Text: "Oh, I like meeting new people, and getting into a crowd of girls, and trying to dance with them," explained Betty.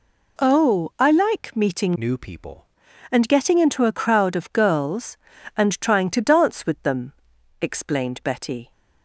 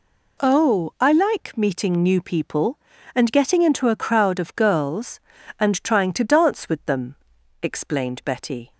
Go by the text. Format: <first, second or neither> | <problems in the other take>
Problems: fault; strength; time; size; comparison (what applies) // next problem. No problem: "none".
second | changes voice from "new" to "people"; from 1.9 to 2.6 s; 0.7 s long